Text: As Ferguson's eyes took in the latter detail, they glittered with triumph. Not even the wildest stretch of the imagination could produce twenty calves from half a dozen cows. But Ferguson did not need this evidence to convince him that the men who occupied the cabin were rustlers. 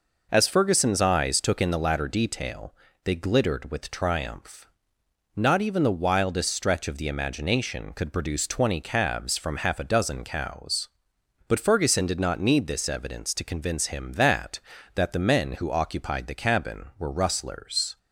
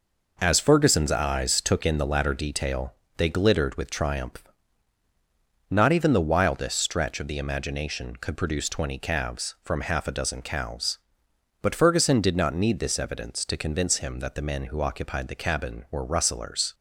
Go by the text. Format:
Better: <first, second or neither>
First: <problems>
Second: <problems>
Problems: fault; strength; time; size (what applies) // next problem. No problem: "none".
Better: second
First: says "that" twice; at 14.9 s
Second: none